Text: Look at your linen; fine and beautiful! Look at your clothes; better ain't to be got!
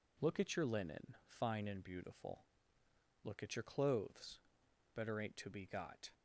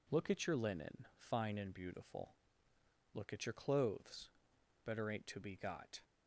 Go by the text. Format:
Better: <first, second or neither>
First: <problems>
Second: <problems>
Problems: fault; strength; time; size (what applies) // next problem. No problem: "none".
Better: neither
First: none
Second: none